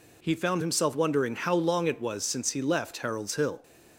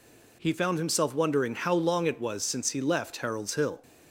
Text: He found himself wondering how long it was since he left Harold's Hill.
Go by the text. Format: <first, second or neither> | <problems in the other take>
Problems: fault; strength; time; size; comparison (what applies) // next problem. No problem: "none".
neither | none